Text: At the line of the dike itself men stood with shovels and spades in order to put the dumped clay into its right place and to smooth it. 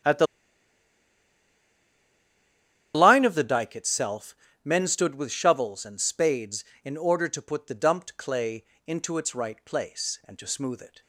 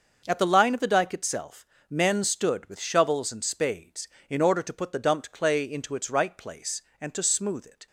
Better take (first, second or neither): second